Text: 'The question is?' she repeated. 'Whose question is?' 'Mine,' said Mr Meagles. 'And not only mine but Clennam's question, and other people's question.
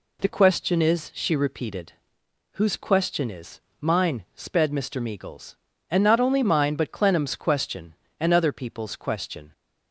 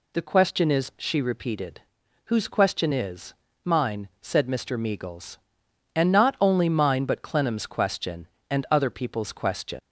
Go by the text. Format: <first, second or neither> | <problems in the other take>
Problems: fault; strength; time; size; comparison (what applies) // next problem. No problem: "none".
second | says "sped" for "said"; at 4.3 s